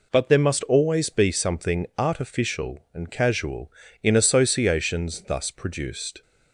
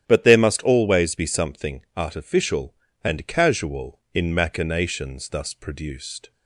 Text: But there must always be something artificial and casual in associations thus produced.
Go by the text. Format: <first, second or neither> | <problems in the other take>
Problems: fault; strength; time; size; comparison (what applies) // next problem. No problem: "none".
first | starts louder than the rest; strong; until 1.1 s; 11 dB // says "machinations" for "associations"; at 4.3 s